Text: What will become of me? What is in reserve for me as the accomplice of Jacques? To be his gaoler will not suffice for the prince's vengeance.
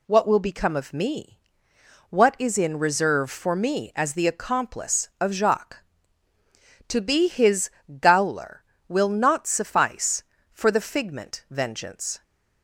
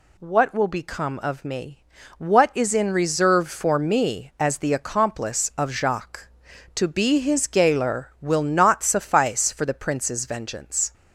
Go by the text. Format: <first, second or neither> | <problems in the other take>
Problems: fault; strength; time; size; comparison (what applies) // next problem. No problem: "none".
second | pauses between "his" and "gaoler"; slight; at 7.7 s; 0.30 s long // says "figment" for "prince's"; at 10.8 s